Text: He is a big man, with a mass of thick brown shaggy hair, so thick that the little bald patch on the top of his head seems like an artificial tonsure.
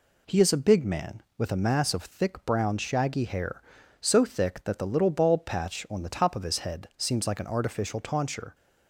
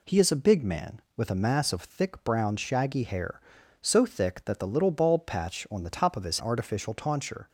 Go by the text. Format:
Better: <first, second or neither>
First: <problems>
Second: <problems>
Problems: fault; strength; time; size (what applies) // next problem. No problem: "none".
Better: first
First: none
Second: skips "head seems like an"; at 6.3 s